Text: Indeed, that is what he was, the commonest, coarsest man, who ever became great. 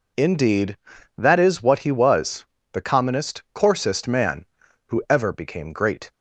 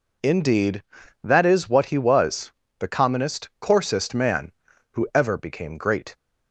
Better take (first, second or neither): neither